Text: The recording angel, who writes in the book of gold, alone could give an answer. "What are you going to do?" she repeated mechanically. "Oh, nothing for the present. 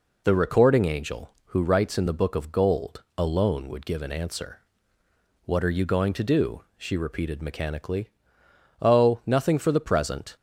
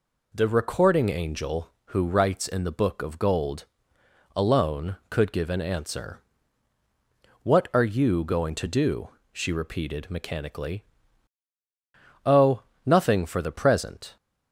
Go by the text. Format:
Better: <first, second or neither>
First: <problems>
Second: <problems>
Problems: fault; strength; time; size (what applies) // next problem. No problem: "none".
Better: second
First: says "would" for "could"; at 3.6 s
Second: none